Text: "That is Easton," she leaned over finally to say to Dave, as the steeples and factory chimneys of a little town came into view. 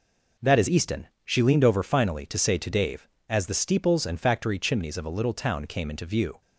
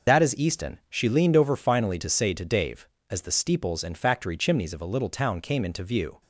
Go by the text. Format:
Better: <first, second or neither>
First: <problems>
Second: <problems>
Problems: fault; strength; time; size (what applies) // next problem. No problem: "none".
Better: first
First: none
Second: loses the start of "That"; at 0.0 s; 65 ms